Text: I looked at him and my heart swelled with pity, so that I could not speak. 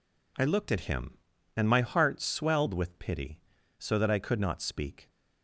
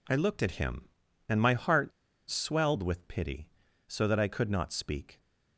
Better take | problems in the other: first | pauses between "heart" and "swelled"; at 1.9 s; 0.39 s long

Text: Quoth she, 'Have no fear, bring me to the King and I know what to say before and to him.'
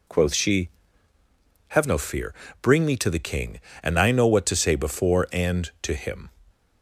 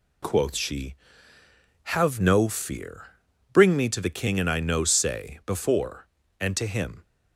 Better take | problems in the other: first | skips "what to"; at 4.8 s

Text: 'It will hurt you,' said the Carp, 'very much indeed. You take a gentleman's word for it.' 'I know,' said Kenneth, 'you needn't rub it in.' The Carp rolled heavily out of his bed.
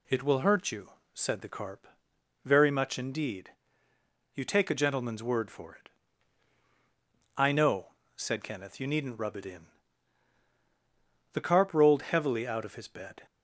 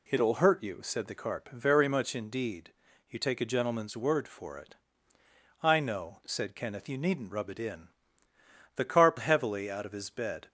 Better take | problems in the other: first | skips "rolled"; at 9.1 s

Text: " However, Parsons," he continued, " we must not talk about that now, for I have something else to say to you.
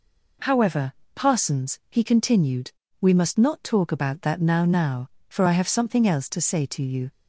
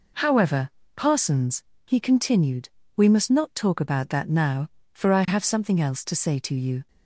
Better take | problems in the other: second | says "now" twice; at 4.6 s

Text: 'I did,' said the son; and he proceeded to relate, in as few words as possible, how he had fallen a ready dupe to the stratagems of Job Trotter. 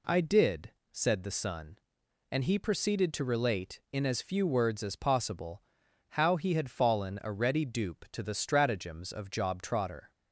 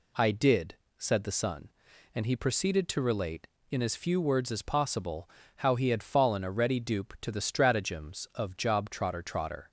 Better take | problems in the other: first | says "Trotter" twice; at 9.2 s

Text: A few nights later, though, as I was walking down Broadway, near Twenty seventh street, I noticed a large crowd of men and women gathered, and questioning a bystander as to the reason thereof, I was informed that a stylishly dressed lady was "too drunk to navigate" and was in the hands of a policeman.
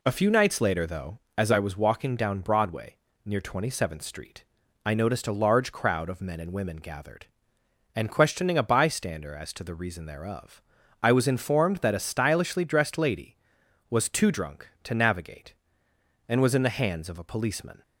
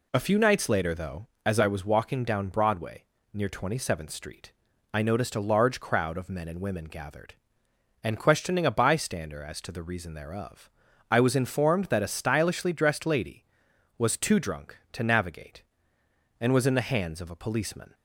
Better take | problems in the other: neither | none

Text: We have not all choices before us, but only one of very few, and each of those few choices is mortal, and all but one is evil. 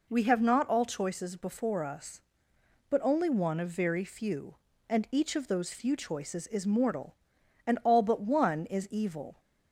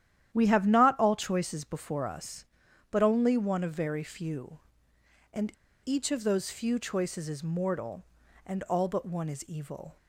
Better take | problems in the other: first | starts louder than the rest; strong; until 1.3 s; 11 dB // pauses between "and" and "each"; slight; at 5.5 s; 0.33 s long

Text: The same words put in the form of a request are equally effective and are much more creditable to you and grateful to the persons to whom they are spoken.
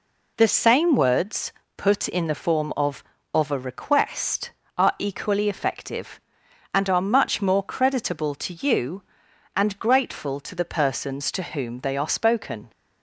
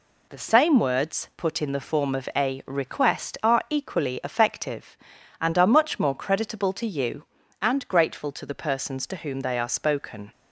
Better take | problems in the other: second | pauses between "words" and "put"; slight; at 1.5 s; 0.24 s long // says "of" twice; at 3.3 s

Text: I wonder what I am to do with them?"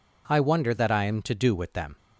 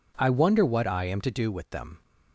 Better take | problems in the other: second | says "that" for "what"; at 0.7 s

